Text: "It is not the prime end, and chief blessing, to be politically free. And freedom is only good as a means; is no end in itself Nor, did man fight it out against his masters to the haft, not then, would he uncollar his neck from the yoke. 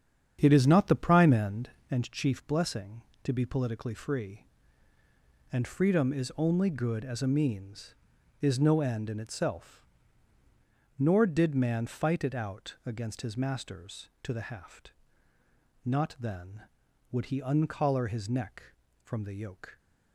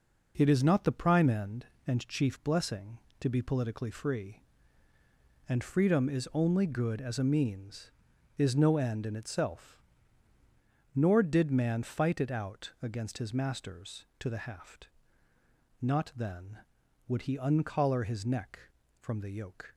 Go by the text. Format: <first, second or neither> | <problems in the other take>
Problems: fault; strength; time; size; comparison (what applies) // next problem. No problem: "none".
second | starts louder than the rest; strong; until 1.9 s; 8.5 dB // pauses between "itself" and "Nor"; at 9.8 s; 1.1 s long; also in the second